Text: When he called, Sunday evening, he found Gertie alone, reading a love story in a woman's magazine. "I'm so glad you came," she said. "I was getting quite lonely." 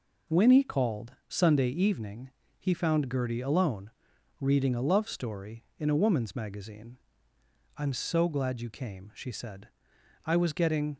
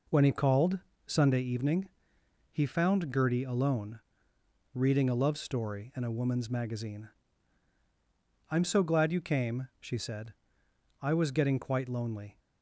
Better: second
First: stops before "quite lonely"; at 10.9 s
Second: none

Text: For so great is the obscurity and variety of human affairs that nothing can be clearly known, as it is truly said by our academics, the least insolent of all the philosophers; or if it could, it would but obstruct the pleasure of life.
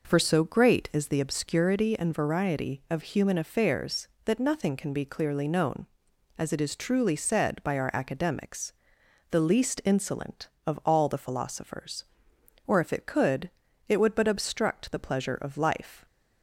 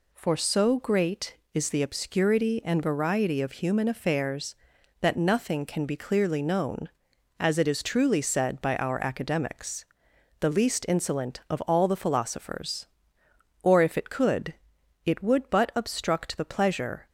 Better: first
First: none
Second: stops before "of life"; at 17.0 s

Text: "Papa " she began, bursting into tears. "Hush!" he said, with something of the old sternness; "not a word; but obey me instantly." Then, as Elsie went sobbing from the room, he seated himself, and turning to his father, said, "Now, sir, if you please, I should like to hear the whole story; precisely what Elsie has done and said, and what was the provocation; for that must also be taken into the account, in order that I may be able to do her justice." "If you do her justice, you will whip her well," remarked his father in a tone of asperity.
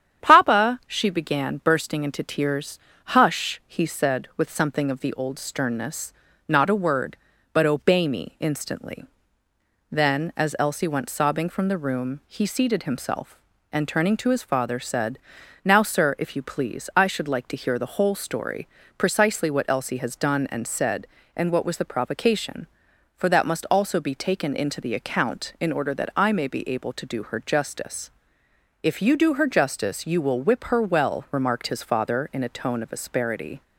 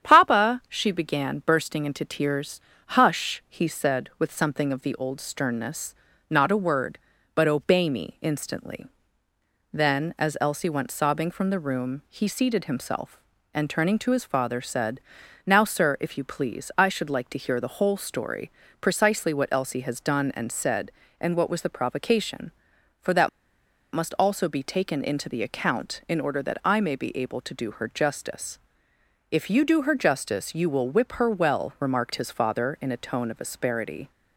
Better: first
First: starts louder than the rest; strong; until 1.2 s; 9 dB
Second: starts louder than the rest; strong; until 1.0 s; 9 dB // pauses between "that" and "must"; noticeable; at 23.2 s; 0.65 s long

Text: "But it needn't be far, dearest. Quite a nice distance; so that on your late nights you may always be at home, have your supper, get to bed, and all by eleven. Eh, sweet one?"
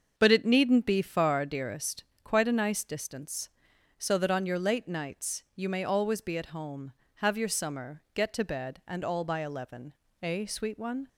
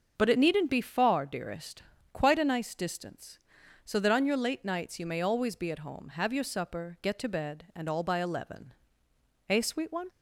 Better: second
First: starts louder than the rest; until 1.1 s; 6.5 dB // says "summer" for "supper"; at 7.4 s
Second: starts louder than the rest; until 1.1 s; 6.5 dB

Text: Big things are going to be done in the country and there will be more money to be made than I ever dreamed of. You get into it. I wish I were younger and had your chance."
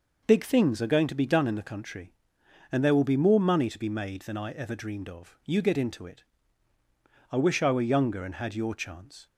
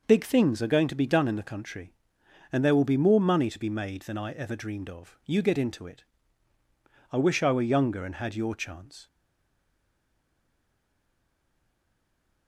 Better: first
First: none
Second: stays silent after the last word; strong; from 9.0 s on; 3.4 s long

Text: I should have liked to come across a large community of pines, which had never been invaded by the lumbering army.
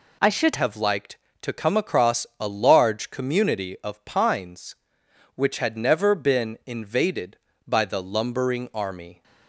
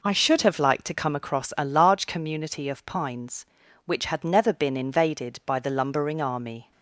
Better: second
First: changes voice at "have"; from 0.5 s on; 8.7 s long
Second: none

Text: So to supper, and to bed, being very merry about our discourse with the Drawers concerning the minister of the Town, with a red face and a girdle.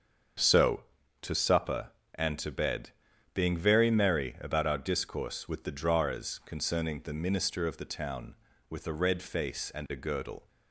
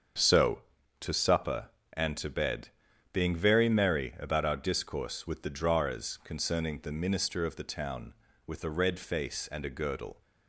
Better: neither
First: starts louder than the rest; until 1.7 s; 7 dB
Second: starts louder than the rest; until 1.5 s; 7 dB

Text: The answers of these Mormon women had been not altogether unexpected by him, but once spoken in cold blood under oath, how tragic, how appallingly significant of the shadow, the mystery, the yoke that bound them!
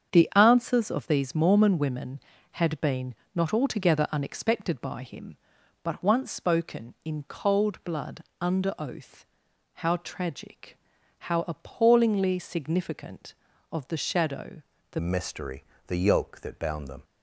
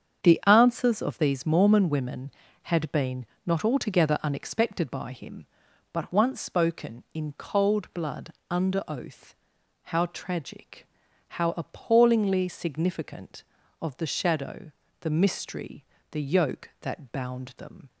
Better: second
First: starts louder than the rest; strong; until 1.1 s; 7.5 dB // pauses between "been" and "not"; slight; at 3.1 s; 0.22 s long // pauses between "blood" and "under"; slight; at 8.2 s; 0.16 s long // changes voice at "mystery"; from 14.9 s on; 2.1 s long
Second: starts louder than the rest; strong; until 1.2 s; 7.5 dB // pauses between "been" and "not"; slight; at 3.2 s; 0.22 s long // pauses between "blood" and "under"; slight; at 8.3 s; 0.16 s long

